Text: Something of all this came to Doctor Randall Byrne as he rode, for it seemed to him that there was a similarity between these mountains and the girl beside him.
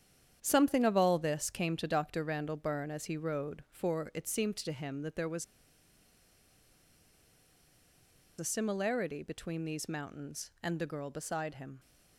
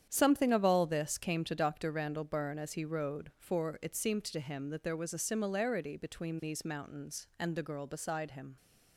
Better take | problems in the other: second | starts louder than the rest; strong; until 1.4 s; 9 dB; strong in the second // pauses between "was" and "a"; strong; at 5.4 s; 2.9 s long

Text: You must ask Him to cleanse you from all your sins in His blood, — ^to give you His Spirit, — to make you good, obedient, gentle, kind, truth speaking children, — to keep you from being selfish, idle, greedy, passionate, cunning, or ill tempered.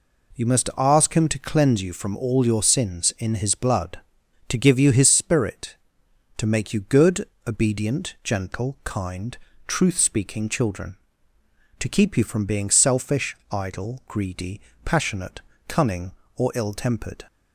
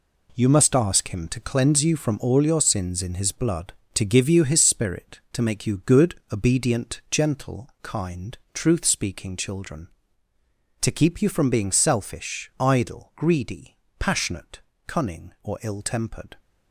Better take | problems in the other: first | gets quieter; strong; throughout; 9.5 dB

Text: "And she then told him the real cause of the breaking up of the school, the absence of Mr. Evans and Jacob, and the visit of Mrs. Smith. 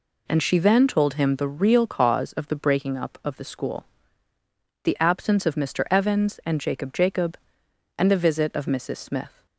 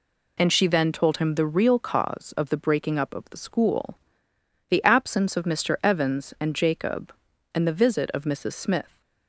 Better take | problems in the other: second | says "Jacob" twice; at 6.9 s

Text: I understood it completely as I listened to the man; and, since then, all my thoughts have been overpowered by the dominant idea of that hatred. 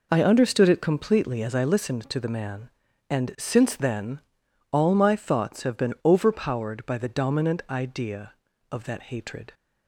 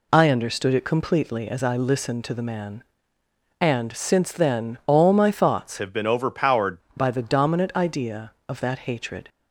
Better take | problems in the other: first | changes voice from "have" to "overpowered"; from 5.7 to 6.7 s; 1.0 s long

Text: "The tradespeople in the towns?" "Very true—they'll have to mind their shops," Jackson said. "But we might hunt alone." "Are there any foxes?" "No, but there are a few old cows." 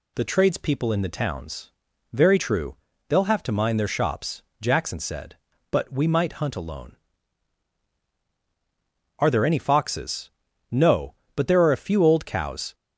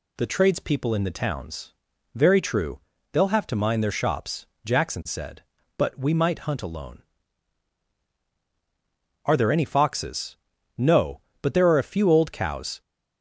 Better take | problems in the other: neither | none

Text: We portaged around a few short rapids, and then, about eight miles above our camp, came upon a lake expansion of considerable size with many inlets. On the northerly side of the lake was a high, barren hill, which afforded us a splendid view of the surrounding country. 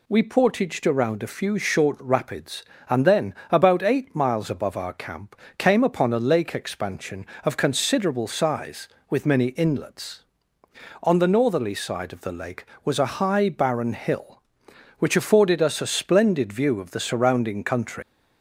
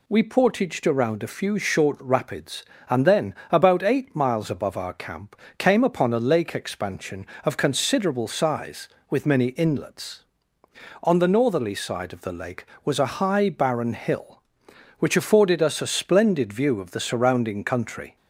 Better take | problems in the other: second | leaves "country" unfinished; at 18.0 s; 130 ms

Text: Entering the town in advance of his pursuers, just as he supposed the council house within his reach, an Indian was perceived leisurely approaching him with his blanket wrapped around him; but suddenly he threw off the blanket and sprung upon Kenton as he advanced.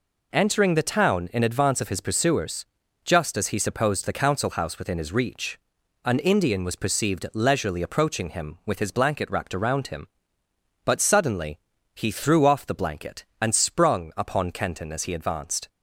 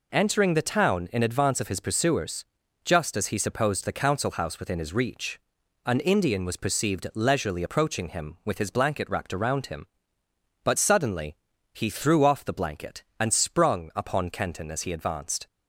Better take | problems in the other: neither | pauses between "suddenly" and "he"; slight; the same in both

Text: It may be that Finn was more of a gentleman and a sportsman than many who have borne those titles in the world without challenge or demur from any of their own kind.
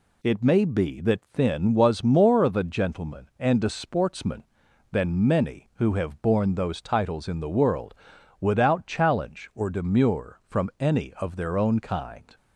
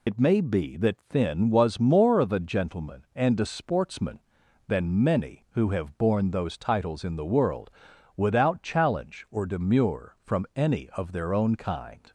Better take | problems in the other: first | loses the start of "It"; at 0.0 s; 70 ms // pauses between "world" and "without"; at 7.7 s; 0.44 s long; also in the first

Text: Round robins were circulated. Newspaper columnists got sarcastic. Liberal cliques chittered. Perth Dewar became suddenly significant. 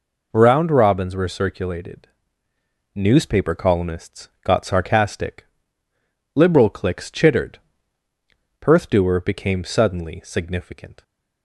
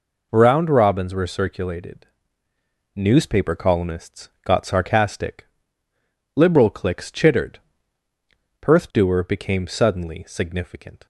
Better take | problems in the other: neither | pauses between "columnists" and "got"; slight; the same in both

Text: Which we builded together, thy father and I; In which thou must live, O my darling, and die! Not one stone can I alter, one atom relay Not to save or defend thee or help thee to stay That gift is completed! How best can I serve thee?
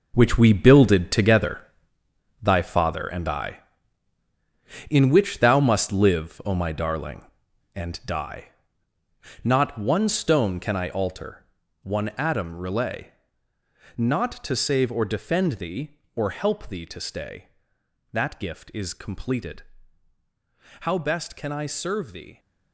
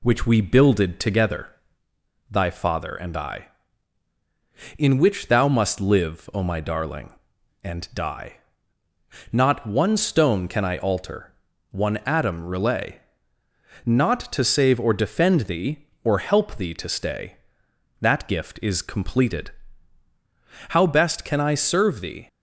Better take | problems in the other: second | gets quieter; strong; throughout; 11.5 dB // pauses between "relay" and "Not"; noticeable; at 13.1 s; 0.86 s long; noticeable in the second

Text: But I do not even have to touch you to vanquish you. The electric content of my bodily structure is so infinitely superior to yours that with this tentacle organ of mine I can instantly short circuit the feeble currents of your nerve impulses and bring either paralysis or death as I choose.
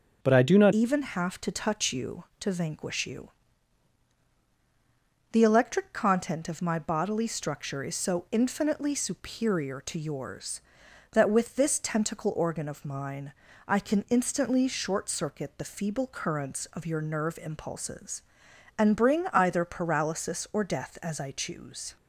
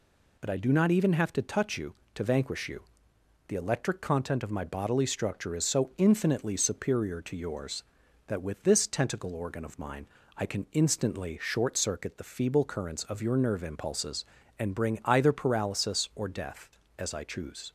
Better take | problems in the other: second | changes voice at "even"; from 0.7 s on; 21.2 s long // pauses between "mine" and "I"; slight; at 13.3 s; 0.36 s long; slight in the second

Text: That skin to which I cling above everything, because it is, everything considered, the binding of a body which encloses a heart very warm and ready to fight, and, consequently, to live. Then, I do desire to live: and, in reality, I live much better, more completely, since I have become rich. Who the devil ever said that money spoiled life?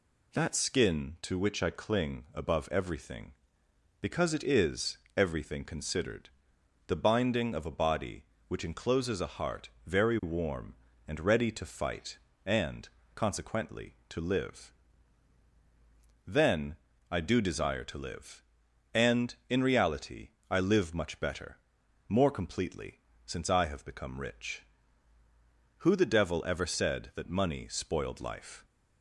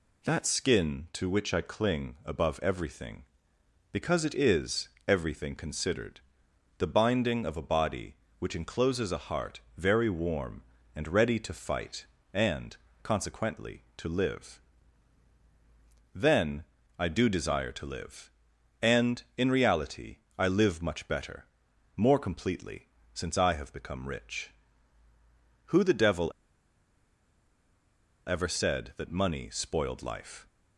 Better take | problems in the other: first | pauses between "heart" and "very"; slight; at 9.5 s; 0.18 s long; slight in the first // pauses between "devil" and "ever"; strong; at 26.3 s; 1.9 s long

